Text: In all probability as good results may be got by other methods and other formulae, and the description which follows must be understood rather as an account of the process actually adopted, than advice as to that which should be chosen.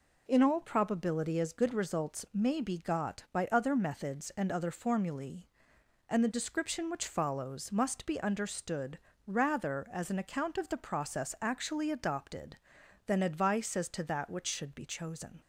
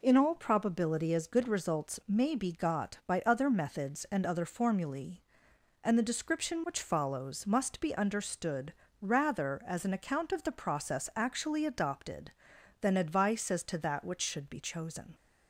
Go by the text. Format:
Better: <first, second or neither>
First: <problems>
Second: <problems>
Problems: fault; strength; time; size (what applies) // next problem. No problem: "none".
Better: neither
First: pauses between "understood" and "rather"; slight; at 8.9 s; 0.28 s long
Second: pauses between "understood" and "rather"; slight; at 8.7 s; 0.28 s long